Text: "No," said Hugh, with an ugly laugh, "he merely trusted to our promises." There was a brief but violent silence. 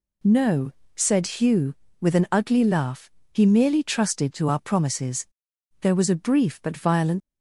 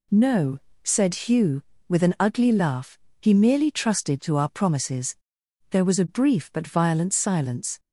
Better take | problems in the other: second | stops before "silence"; at 7.2 s

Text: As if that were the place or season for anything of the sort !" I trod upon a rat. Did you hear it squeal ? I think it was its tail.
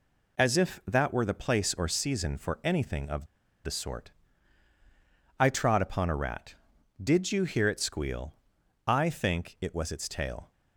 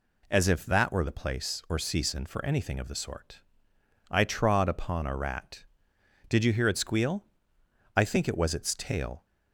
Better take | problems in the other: second | pauses between "of" and "the"; at 3.2 s; 0.38 s long

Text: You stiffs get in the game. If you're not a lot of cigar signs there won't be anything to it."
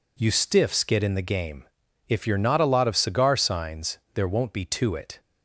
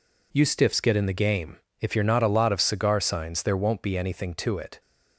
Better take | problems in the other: second | pauses between "signs" and "there"; slight; at 3.9 s; 0.16 s long // skips "anything"; at 4.6 s

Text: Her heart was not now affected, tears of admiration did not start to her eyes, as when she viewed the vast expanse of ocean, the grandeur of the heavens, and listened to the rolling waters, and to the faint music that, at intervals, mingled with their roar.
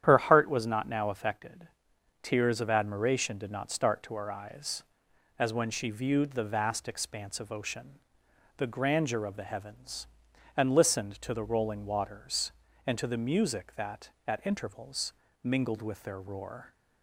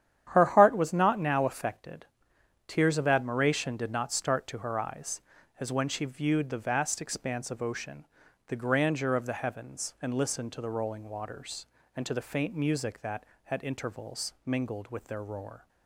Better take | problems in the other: second | starts louder than the rest; strong; until 1.0 s; 10 dB; strong in the second // skips "faint"; at 13.1 s

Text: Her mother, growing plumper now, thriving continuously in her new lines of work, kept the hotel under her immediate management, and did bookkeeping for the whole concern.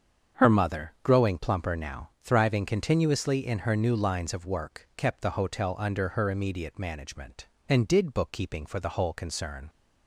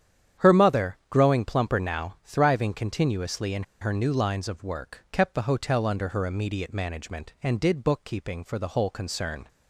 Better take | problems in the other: first | starts louder than the rest; strong; until 1.5 s; 9 dB; strong in the first // pauses between "in" and "her"; slight; at 3.6 s; 0.17 s long

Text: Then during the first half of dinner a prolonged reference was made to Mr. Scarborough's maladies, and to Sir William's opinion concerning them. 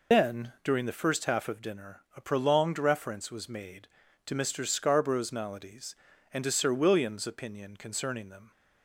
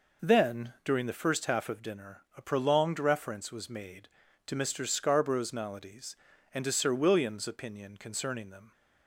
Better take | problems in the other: second | loses the start of "Then"; at 0.1 s; 100 ms // pauses between "dinner" and "a"; slight; at 2.0 s; 0.16 s long; slight in the second

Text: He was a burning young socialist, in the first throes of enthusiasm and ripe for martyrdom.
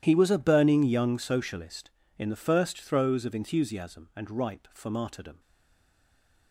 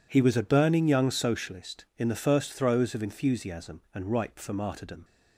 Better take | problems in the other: second | starts louder than the rest; strong; until 1.0 s; 11.5 dB // stays silent after the last word; from 5.3 s on; 1.2 s long

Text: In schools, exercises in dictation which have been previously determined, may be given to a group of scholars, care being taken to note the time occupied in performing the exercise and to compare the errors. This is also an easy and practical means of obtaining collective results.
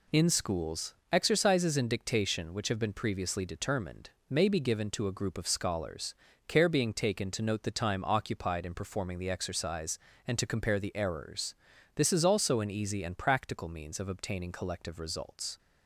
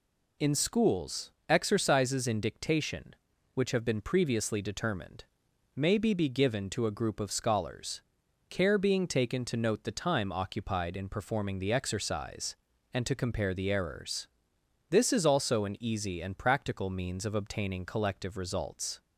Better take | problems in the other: first | says "be" twice; at 6.1 s

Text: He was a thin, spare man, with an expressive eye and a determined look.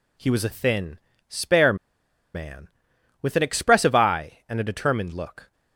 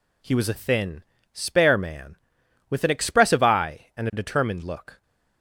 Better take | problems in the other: second | pauses between "spare" and "man"; noticeable; at 1.7 s; 0.59 s long

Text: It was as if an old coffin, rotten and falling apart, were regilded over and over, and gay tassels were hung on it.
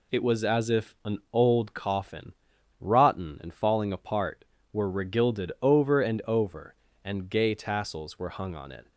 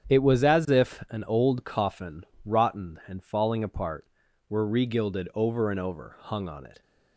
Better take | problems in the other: first | starts louder than the rest; strong; until 1.1 s; 8.5 dB // skips "and gay tassels were"; at 6.1 s

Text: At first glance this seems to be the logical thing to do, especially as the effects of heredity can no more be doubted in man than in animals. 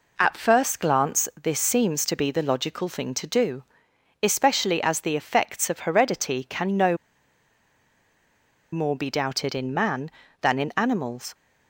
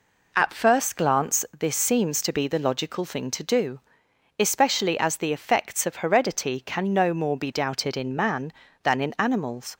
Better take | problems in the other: second | pauses between "no" and "more"; strong; at 6.9 s; 1.7 s long

